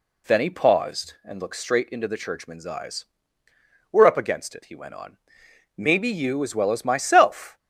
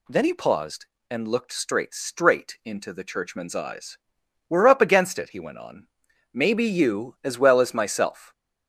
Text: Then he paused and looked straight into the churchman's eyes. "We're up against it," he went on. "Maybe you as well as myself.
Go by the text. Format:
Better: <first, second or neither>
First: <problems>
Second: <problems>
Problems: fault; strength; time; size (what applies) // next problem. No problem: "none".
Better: first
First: none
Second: says "straight" twice; at 1.9 s